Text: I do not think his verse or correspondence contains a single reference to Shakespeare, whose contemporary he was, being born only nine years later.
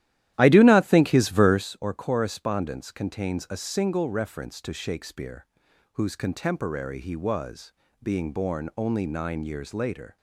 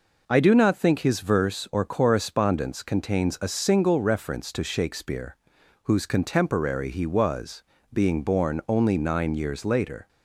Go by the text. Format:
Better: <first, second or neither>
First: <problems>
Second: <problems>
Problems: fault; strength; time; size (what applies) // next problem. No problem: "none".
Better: second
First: starts louder than the rest; strong; until 1.7 s; 13 dB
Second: none